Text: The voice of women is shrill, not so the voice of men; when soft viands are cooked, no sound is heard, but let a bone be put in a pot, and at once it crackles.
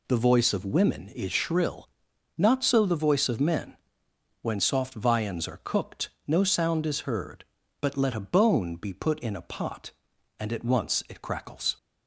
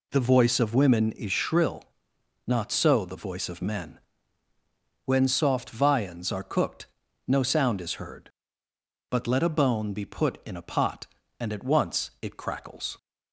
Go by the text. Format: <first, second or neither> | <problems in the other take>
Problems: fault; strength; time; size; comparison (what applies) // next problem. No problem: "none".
neither | none